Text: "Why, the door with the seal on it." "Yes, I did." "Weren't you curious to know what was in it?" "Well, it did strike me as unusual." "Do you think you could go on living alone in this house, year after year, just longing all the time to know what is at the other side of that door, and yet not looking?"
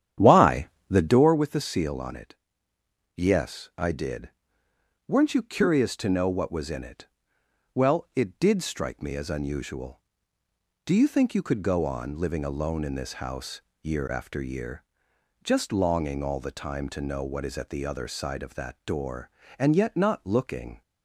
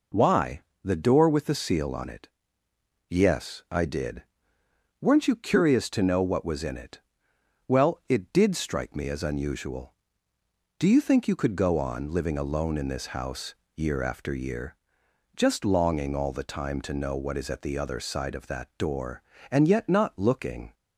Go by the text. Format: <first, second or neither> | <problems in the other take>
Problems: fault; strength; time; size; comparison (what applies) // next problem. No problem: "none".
second | starts louder than the rest; strong; until 1.3 s; 10 dB